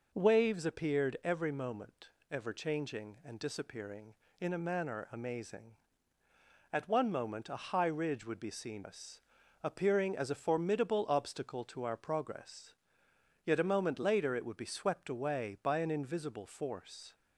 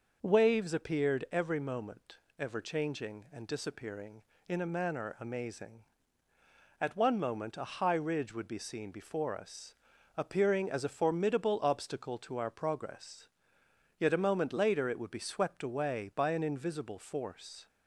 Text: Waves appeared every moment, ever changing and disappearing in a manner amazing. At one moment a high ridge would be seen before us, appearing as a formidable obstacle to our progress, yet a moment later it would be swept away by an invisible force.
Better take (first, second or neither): second